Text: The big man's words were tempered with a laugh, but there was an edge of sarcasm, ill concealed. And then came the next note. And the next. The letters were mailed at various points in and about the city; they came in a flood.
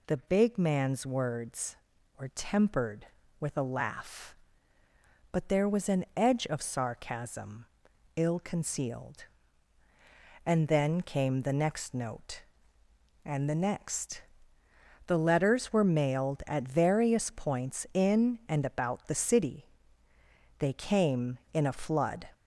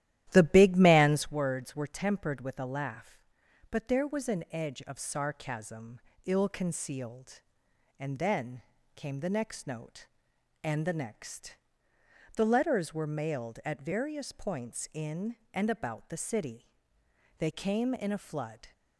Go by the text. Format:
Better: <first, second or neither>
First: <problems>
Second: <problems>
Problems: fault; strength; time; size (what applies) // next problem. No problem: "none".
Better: first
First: none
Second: starts louder than the rest; strong; until 1.4 s; 13 dB // pauses between "then" and "came"; slight; at 8.5 s; 0.34 s long